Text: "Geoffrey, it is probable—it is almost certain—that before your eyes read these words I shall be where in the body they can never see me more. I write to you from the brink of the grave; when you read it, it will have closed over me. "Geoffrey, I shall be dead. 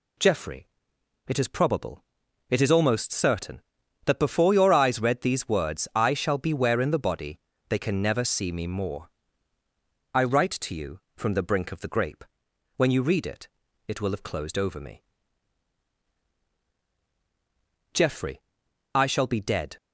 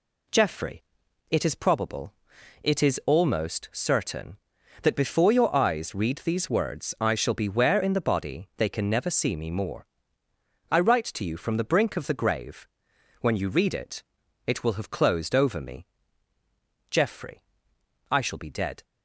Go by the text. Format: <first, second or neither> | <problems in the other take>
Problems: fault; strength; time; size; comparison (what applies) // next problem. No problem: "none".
second | pauses between "body" and "they"; slight; at 7.3 s; 0.30 s long // says "grape" for "grave"; at 11.8 s